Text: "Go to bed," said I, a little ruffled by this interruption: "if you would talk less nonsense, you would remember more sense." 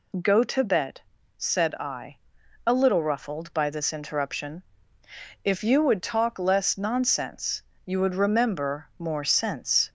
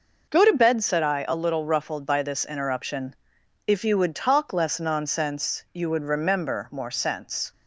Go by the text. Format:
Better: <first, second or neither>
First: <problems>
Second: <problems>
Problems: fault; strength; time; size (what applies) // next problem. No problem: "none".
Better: first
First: none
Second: gets quieter; throughout; 7 dB